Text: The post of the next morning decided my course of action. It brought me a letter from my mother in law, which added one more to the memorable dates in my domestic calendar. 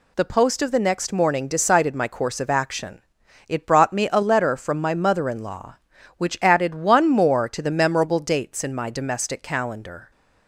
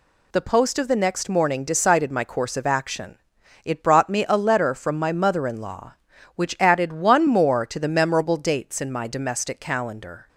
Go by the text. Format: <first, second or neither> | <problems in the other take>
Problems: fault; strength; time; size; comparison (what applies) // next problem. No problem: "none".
neither | none